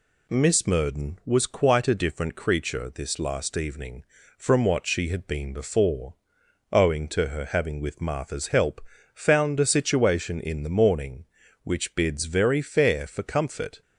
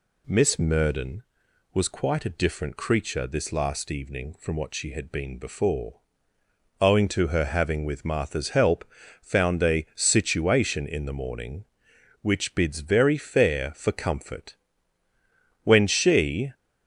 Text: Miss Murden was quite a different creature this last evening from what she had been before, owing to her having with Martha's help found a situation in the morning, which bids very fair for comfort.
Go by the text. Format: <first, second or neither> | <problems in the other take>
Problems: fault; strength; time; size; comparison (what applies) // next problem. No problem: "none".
first | pauses between "help" and "found"; at 8.8 s; 0.38 s long; slight in the first // goes on to say "When she"; noticeable; from 15.6 s on; 0.90 s long